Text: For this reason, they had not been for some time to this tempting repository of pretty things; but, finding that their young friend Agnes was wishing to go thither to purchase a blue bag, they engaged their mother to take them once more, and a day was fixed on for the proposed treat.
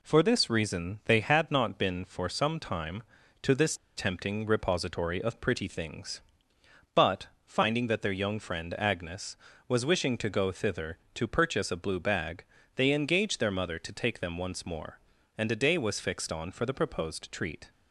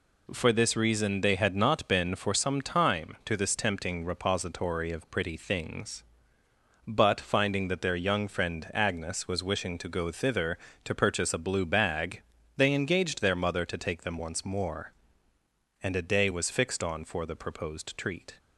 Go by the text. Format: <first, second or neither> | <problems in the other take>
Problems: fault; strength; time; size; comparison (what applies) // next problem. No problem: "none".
second | pauses between "this" and "tempting"; slight; at 3.7 s; 0.21 s long